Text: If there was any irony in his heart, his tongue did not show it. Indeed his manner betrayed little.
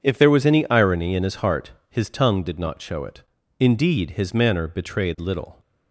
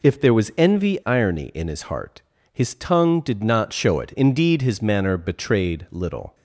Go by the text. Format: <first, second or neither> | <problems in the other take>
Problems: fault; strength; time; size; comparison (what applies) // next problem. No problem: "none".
first | says "envy" for "any"; at 0.5 s